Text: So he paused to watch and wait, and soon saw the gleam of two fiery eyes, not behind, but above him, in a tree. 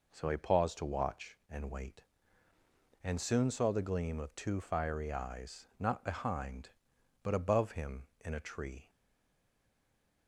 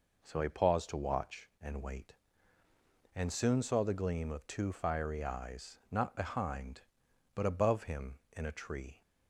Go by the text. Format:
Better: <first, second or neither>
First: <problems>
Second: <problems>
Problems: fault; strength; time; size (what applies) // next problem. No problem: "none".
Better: second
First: stays silent after the last word; noticeable; from 8.8 s on; 1.4 s long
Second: none